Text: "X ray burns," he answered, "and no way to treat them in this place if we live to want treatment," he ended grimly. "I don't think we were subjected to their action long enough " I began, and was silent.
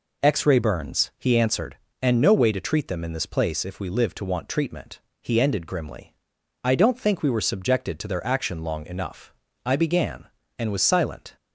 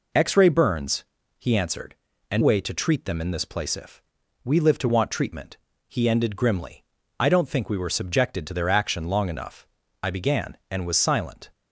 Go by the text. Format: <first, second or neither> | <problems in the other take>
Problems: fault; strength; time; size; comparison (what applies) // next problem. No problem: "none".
first | skips "no"; at 2.4 s // pauses between "if" and "we"; at 4.0 s; 0.40 s long